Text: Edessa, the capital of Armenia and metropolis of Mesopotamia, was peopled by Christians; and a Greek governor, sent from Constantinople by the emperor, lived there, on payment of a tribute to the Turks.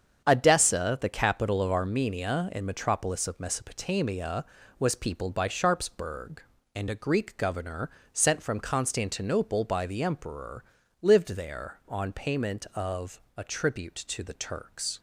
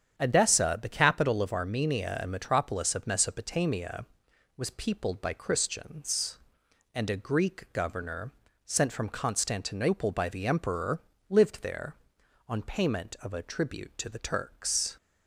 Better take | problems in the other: second | starts louder than the rest; strong; until 1.2 s; 8 dB; strong in the second // says "Sharpsburg" for "Christians"; at 5.4 s // pauses between "of" and "a"; slight; at 13.1 s; 0.16 s long

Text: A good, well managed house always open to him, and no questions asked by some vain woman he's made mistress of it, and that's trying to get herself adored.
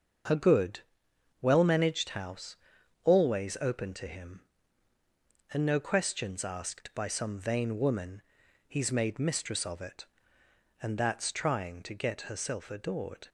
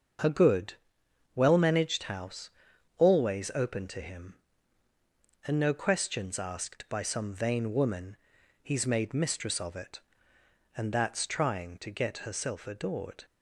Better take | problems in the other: neither | starts louder than the rest; the same in both // pauses between "house" and "always"; noticeable; the same in both // pauses between "woman" and "he's"; the same in both

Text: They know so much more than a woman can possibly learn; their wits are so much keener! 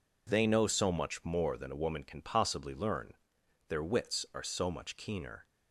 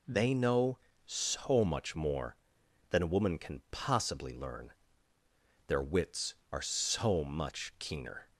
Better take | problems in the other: neither | none

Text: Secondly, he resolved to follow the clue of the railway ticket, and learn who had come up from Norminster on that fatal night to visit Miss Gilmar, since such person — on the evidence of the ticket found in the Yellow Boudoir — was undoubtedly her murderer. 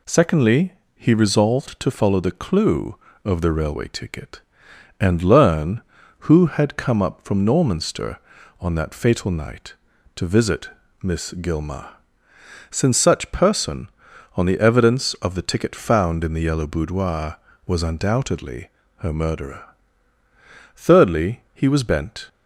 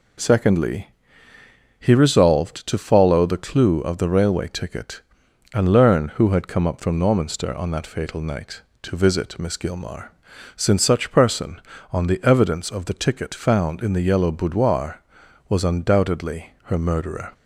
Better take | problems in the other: second | pauses between "visit" and "Miss"; slight; at 10.6 s; 0.32 s long // pauses between "undoubtedly" and "her"; slight; at 18.6 s; 0.28 s long // goes on to say "Thirdly he was bent"; from 20.7 s on; 1.5 s long

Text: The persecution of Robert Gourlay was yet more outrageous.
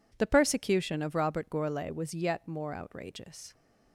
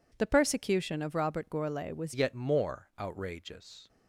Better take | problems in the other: first | changes voice at "yet"; from 2.1 s on; 1.7 s long

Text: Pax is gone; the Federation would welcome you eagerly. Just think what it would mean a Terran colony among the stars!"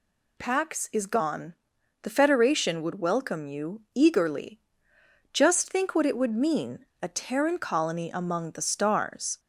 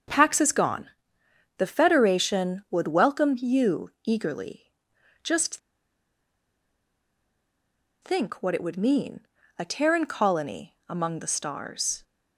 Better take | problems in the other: first | starts louder than the rest; noticeable; until 1.7 s; 6 dB // pauses between "Just" and "think"; strong; at 5.5 s; 2.4 s long // pauses between "mean" and "a"; slight; at 9.2 s; 0.36 s long; slight in the first

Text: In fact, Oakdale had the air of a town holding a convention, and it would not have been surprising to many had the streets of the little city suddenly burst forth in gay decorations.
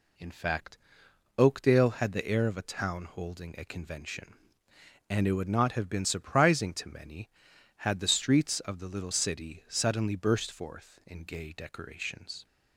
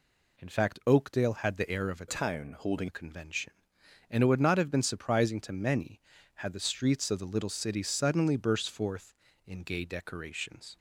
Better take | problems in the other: first | changes voice from "town" to "holding"; from 2.0 to 2.8 s; 0.8 s long

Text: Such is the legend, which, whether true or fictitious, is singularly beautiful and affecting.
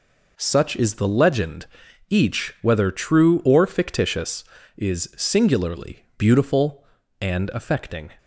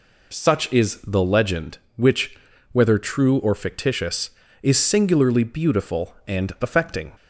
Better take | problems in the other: second | says "each" for "which"; at 2.0 s

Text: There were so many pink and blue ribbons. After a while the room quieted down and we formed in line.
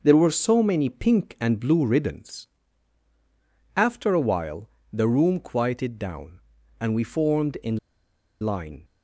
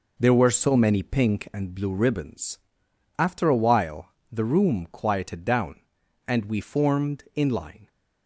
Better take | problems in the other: second | pauses between "while" and "the"; slight; at 4.6 s; 0.24 s long; slight in the second // pauses between "in" and "line"; noticeable; at 7.7 s; 0.64 s long

